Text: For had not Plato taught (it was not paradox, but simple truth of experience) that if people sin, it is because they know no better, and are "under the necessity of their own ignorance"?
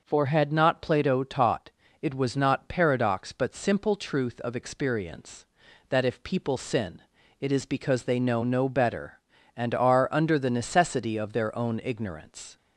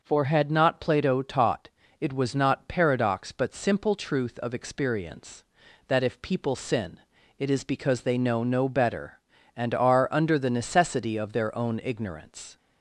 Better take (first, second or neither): neither